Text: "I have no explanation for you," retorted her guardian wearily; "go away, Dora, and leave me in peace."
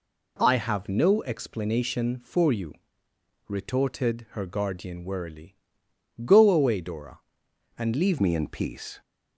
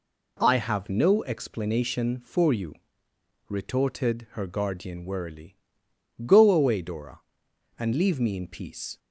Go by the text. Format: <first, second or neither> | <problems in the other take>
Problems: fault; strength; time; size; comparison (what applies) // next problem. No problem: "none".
second | changes voice at "me"; from 8.2 s on; 0.8 s long